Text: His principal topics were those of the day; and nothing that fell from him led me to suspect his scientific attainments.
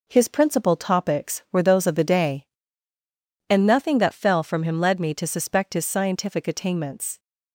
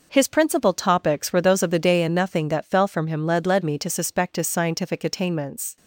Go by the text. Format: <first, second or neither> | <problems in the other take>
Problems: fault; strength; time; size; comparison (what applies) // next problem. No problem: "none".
first | says "led" twice; at 3.4 s